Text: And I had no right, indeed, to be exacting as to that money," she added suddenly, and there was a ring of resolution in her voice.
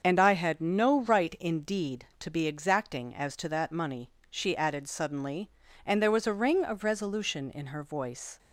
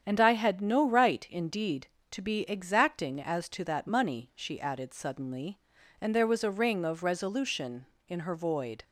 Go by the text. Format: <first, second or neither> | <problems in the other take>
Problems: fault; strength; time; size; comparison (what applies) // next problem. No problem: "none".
first | starts louder than the rest; strong; until 1.0 s; 8.5 dB; also in the first // says "void" for "voice"; at 8.3 s